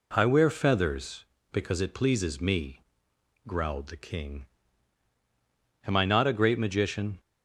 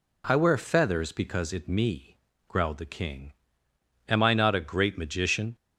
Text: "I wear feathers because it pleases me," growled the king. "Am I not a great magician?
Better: first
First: none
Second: skips "pleases"; at 1.6 s

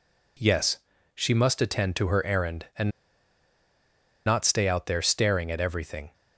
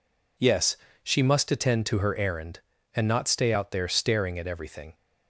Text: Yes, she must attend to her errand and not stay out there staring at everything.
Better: second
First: pauses between "and" and "not"; strong; at 2.8 s; 1.3 s long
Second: none

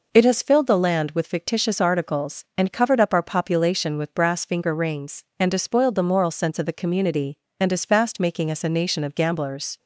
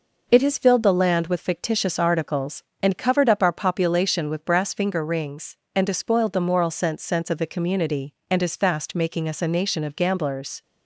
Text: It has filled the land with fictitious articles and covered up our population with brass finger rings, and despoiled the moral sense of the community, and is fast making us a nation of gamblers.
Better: first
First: none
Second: says "sense" twice; at 7.0 s

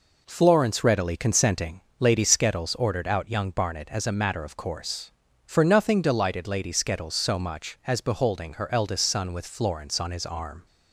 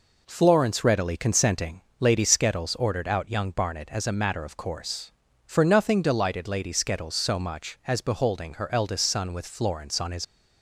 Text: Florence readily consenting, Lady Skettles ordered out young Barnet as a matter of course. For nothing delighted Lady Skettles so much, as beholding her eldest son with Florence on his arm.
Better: first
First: none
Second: stops before "arm"; at 10.2 s

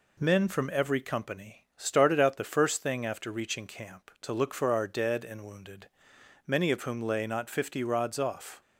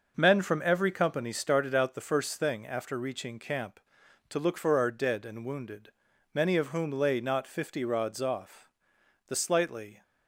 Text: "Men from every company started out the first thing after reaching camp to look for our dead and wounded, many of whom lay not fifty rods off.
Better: first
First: none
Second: goes on to say "The slightly"; noticeable; from 9.2 s on; 0.76 s long

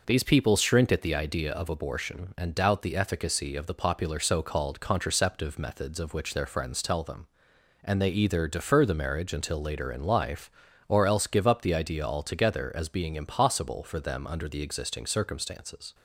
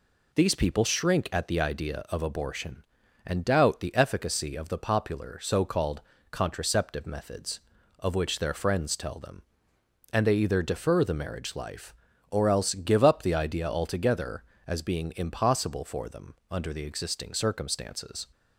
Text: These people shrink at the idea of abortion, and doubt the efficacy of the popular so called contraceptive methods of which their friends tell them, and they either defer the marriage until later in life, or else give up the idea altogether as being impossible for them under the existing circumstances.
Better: first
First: none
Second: pauses between "called" and "contraceptive"; slight; at 6.0 s; 0.30 s long // skips "until later in"; at 11.5 s // pauses between "them" and "under"; slight; at 16.3 s; 0.16 s long

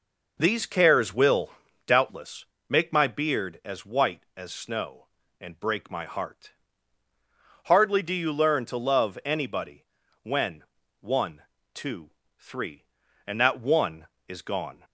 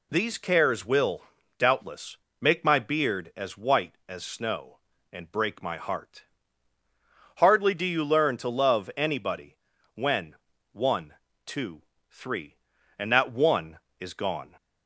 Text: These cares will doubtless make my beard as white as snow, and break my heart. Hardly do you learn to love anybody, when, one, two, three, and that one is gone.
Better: second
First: starts louder than the rest; noticeable; until 2.1 s; 5.5 dB // pauses between "will" and "doubtless"; at 1.4 s; 0.38 s long // pauses between "doubtless" and "make"; slight; at 2.4 s; 0.24 s long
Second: pauses between "will" and "doubtless"; at 1.2 s; 0.38 s long // pauses between "doubtless" and "make"; slight; at 2.1 s; 0.24 s long

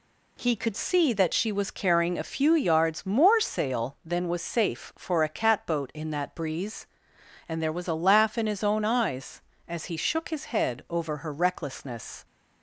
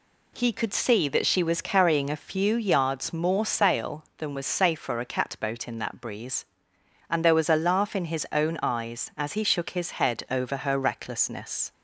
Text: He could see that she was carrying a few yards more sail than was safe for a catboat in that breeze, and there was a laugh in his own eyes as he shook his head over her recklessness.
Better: second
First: changes voice at "see"; from 0.7 s on; 11.5 s long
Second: none

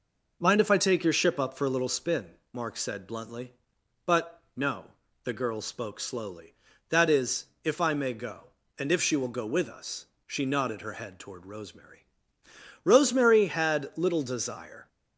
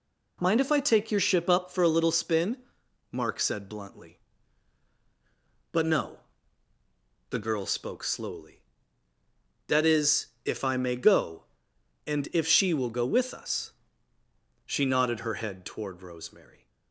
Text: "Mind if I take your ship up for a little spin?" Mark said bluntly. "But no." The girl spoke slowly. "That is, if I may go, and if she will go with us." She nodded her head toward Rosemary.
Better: second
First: pauses between "But" and "no"; slight; at 4.3 s; 0.16 s long // goes on to say "Rosemary had little desire"; strong; from 12.8 s on; 2.0 s long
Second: none

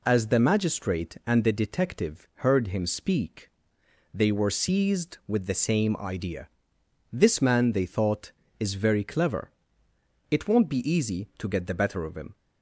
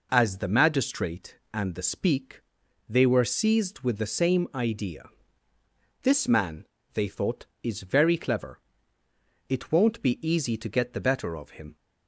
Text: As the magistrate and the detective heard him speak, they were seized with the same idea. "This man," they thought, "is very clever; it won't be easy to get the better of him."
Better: first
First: none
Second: skips "detective heard him"; at 1.8 s

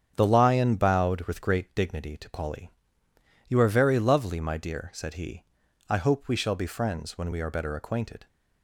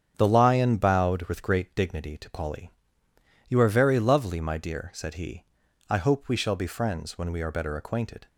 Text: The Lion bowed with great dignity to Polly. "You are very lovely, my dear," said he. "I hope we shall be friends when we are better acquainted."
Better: neither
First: starts louder than the rest; strong; until 1.1 s; 8 dB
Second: starts louder than the rest; strong; until 1.1 s; 8 dB

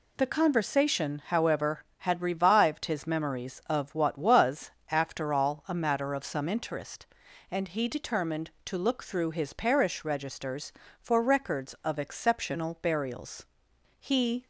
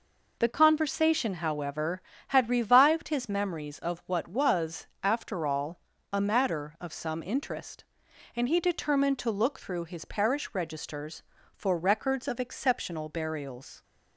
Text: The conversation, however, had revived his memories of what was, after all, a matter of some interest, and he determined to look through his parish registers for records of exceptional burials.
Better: second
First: goes on to say "He"; slight; from 13.9 s on; 0.48 s long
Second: none

